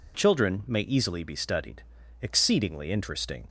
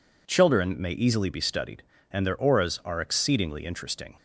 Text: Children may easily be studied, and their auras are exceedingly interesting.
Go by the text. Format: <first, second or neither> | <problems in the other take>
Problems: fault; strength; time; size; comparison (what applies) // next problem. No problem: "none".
second | skips "and their auras are"; at 2.0 s